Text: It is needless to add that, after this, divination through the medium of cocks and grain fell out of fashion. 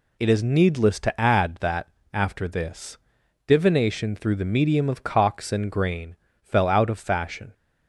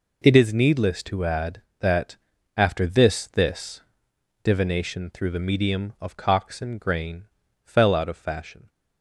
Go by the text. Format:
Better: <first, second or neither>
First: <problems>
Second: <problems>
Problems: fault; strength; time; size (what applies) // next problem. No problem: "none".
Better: first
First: pauses between "grain" and "fell"; slight; at 6.1 s; 0.26 s long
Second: says "this" twice; at 3.2 s // pauses between "grain" and "fell"; at 7.2 s; 0.38 s long